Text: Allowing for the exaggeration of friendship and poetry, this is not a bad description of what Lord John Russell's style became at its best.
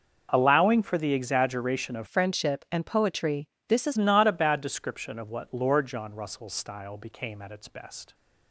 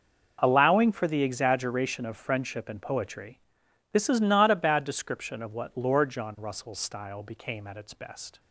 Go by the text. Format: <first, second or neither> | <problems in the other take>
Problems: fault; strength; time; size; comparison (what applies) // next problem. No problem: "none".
second | changes voice from "friendship" to "is"; from 2.0 to 3.9 s; 1.9 s long